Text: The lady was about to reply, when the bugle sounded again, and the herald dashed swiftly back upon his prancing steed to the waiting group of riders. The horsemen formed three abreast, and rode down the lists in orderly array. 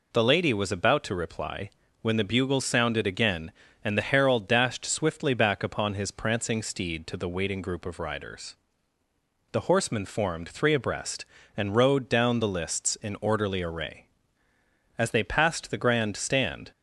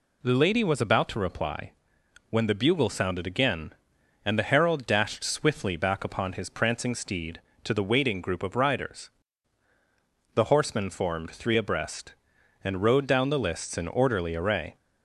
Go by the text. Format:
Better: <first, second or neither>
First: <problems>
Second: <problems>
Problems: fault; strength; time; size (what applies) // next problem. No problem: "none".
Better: second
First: goes on to say "As they passed the grand stand"; strong; from 14.9 s on; 1.7 s long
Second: none